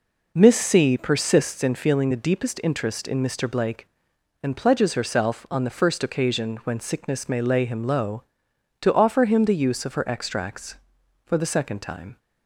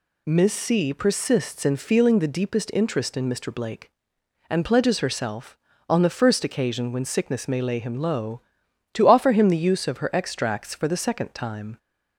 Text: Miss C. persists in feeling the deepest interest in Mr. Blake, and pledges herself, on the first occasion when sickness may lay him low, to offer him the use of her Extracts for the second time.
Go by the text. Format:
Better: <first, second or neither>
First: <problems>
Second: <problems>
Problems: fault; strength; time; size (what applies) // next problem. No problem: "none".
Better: neither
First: none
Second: none